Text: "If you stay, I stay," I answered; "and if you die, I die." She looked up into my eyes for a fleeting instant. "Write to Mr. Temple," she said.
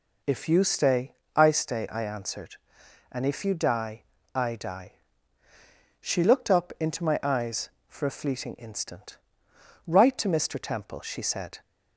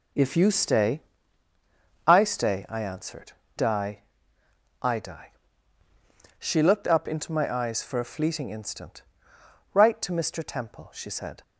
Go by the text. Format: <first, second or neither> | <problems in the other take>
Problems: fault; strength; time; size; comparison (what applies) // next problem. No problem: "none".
first | skips "and if you"; at 3.4 s